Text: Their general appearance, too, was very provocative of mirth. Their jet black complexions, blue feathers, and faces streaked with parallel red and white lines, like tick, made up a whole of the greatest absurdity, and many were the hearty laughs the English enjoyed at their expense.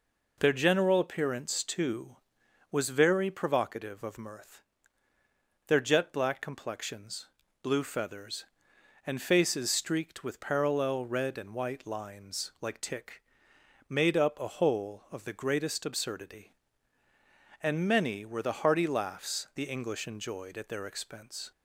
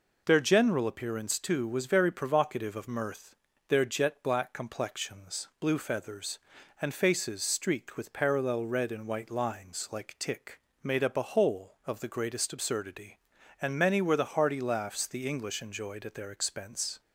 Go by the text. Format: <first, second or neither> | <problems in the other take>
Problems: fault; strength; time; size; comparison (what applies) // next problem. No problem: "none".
neither | none